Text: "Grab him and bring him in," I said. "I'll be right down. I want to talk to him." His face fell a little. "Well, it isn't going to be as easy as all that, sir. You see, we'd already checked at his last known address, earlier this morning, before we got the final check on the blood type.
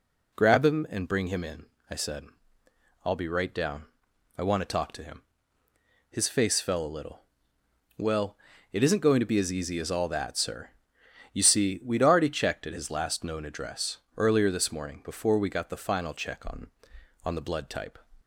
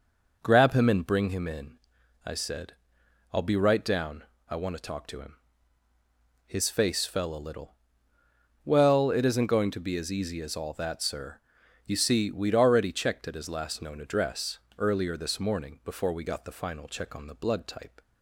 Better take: second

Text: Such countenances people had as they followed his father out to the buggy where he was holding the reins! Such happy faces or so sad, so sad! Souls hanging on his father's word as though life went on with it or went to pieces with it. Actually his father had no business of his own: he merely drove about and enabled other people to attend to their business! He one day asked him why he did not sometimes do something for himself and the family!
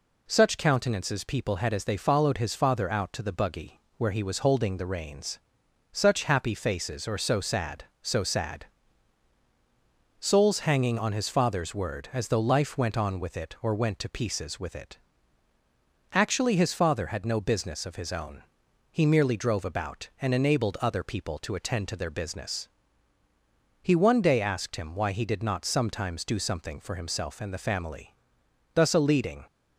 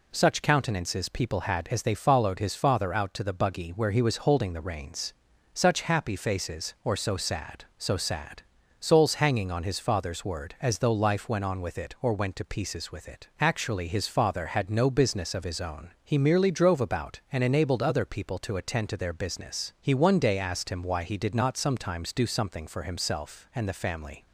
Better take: second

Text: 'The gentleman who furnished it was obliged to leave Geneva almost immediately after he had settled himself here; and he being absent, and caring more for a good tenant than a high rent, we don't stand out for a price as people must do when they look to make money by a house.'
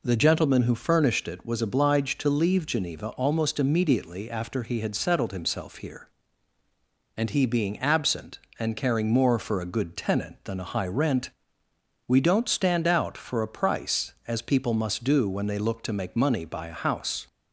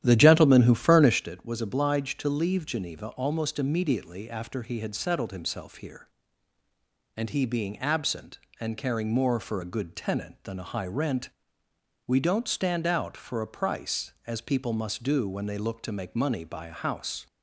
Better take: first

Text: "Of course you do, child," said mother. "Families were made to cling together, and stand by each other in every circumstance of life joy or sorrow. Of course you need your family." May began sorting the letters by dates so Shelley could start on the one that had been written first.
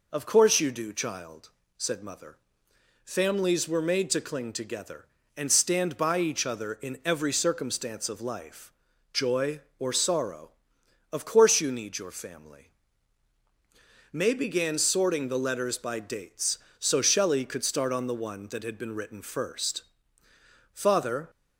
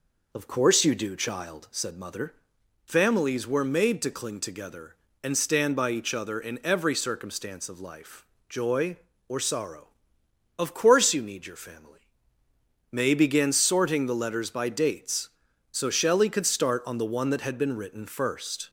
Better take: second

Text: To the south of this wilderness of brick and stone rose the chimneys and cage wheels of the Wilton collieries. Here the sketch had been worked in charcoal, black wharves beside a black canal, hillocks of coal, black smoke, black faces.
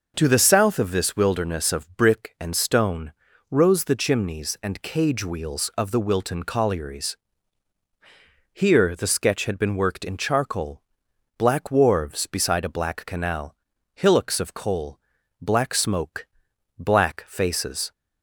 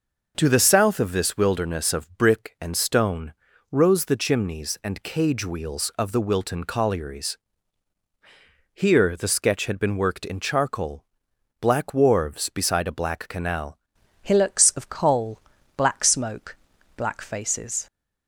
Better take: first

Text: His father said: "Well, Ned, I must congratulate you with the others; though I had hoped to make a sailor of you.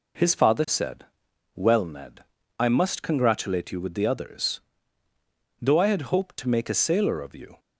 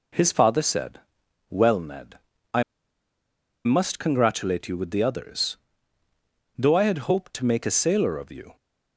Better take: first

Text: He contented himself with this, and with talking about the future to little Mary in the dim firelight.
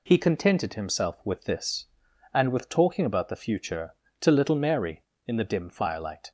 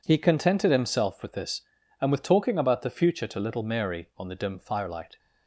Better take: first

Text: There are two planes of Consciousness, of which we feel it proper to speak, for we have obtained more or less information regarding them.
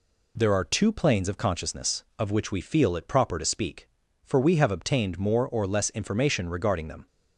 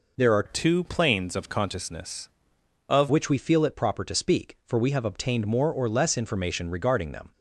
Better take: first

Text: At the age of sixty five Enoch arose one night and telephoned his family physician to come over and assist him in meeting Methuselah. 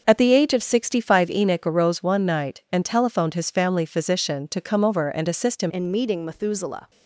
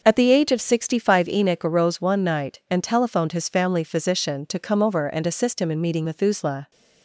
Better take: second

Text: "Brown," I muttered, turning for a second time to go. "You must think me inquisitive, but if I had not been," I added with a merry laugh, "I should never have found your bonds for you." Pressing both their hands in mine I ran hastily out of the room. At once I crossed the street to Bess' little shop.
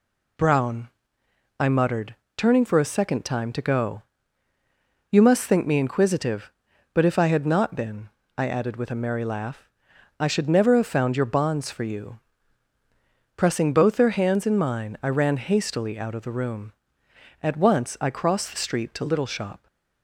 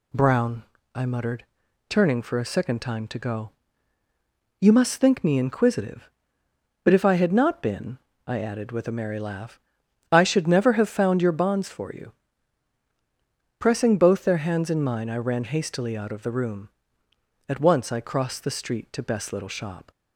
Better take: second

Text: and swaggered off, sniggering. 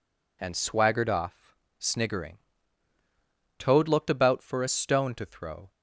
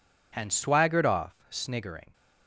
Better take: second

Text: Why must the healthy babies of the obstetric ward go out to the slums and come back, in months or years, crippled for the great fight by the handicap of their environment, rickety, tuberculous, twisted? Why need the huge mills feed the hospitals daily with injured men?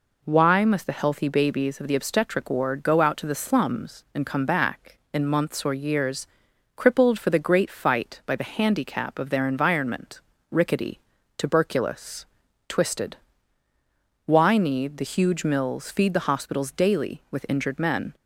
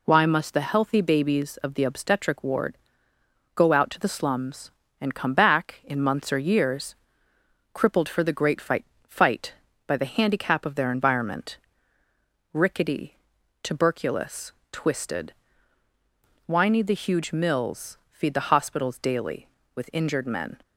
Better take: first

